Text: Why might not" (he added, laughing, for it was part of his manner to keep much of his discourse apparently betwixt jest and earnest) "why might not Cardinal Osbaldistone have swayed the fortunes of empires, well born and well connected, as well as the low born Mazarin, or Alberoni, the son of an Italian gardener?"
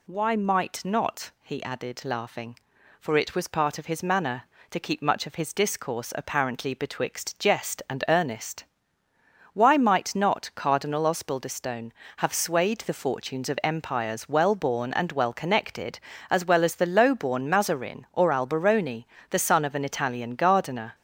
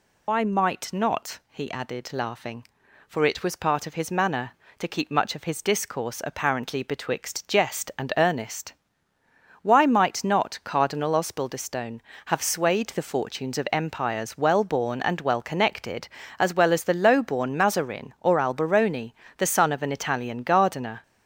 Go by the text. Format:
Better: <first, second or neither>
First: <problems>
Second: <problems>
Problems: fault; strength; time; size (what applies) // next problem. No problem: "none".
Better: first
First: none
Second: loses the start of "Why"; at 0.2 s; 125 ms